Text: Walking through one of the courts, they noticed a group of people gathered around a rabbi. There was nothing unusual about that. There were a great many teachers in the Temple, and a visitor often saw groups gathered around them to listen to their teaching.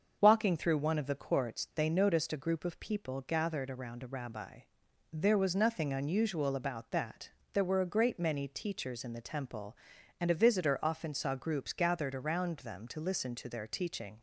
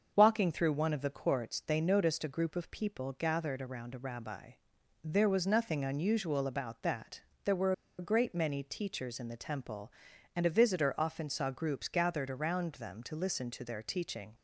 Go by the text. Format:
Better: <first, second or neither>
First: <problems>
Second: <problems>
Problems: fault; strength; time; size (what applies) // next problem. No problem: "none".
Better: first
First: starts louder than the rest; until 1.2 s; 6.5 dB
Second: starts louder than the rest; until 1.1 s; 6.5 dB // pauses between "were" and "a"; slight; at 7.7 s; 0.25 s long